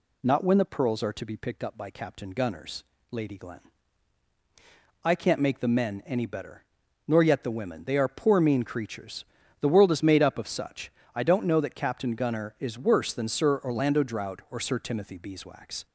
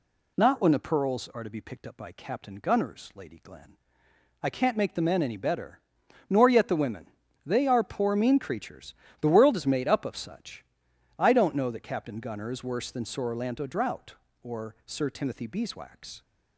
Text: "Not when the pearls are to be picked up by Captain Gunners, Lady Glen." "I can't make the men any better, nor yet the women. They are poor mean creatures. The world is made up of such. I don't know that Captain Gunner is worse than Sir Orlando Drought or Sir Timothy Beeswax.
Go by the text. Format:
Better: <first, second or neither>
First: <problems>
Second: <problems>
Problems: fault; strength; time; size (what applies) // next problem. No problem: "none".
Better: neither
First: none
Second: none